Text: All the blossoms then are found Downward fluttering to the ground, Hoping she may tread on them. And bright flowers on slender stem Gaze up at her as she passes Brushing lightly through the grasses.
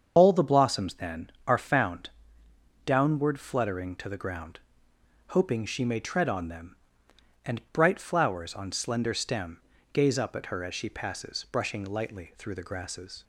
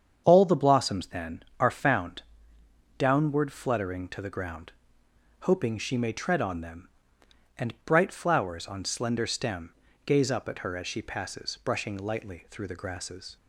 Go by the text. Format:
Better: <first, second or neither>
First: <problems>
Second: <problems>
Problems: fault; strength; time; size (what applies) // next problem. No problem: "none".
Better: second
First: loses the start of "All"; at 0.1 s; 25 ms // starts louder than the rest; strong; until 1.1 s; 7 dB // pauses between "found" and "Downward"; noticeable; at 2.0 s; 0.74 s long // pauses between "stem" and "Gaze"; slight; at 9.6 s; 0.32 s long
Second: starts louder than the rest; strong; until 1.2 s; 7.5 dB // pauses between "found" and "Downward"; noticeable; at 2.2 s; 0.74 s long // pauses between "stem" and "Gaze"; slight; at 9.7 s; 0.32 s long